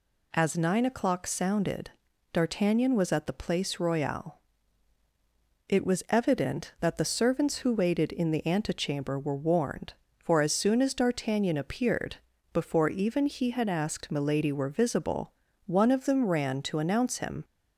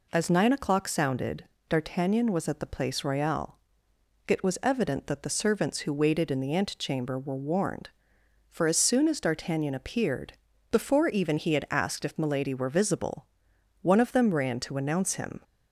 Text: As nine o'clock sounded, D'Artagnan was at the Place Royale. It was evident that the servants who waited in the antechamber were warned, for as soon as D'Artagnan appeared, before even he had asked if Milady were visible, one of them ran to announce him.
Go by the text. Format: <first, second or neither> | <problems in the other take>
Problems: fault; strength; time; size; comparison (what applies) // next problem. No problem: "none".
second | skips "if"; at 14.1 s